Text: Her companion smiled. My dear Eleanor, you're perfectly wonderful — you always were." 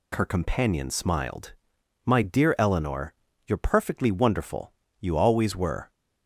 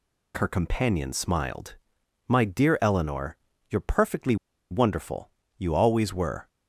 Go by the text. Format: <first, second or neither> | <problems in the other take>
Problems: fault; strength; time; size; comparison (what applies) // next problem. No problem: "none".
first | pauses between "perfectly" and "wonderful"; slight; at 4.3 s; 0.35 s long